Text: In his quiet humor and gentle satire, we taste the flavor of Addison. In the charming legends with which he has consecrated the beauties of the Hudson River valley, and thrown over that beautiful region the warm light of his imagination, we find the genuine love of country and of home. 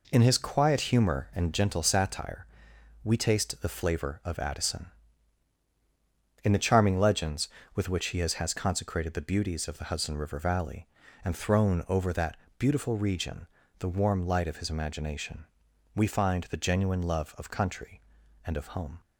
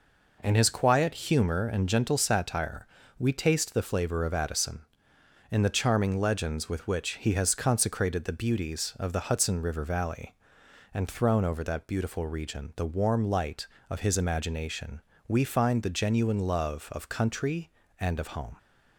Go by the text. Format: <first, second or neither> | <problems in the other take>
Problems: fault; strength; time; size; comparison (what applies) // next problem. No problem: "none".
second | says "has" twice; at 8.3 s // pauses between "that" and "beautiful"; slight; at 12.3 s; 0.22 s long // pauses between "region" and "the"; slight; at 13.4 s; 0.32 s long